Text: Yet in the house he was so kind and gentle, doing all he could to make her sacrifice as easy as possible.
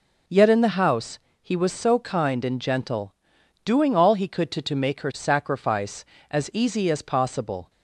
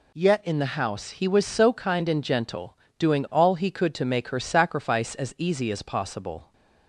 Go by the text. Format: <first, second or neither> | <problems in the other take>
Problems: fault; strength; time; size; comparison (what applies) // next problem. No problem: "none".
second | pauses between "house" and "he"; slight; at 1.1 s; 0.24 s long // says "to" twice; at 4.6 s